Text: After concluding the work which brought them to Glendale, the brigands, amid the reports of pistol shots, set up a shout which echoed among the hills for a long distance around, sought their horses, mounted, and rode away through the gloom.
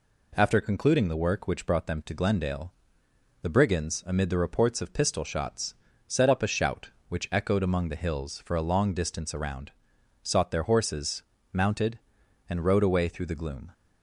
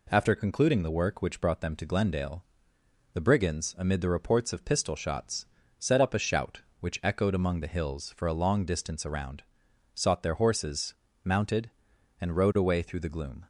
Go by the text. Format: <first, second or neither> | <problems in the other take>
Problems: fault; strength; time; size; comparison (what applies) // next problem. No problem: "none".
neither | none